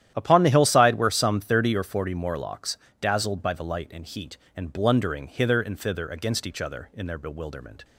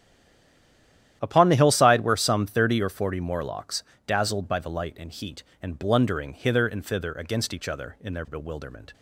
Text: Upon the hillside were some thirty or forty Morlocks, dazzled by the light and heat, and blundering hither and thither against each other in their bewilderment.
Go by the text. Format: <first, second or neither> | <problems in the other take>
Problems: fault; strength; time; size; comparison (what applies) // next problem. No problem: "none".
first | stays silent before the first word; noticeable; until 1.2 s; 1.2 s long // starts louder than the rest; strong; until 2.2 s; 11.5 dB; strong in the first